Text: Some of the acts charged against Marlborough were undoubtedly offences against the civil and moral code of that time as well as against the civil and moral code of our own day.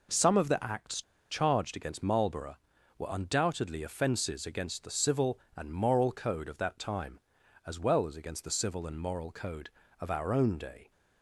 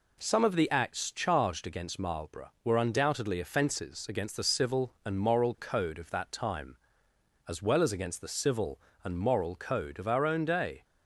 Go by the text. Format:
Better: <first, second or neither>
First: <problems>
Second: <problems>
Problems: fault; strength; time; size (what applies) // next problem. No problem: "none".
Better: second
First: pauses between "acts" and "charged"; slight; at 1.0 s; 0.27 s long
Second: none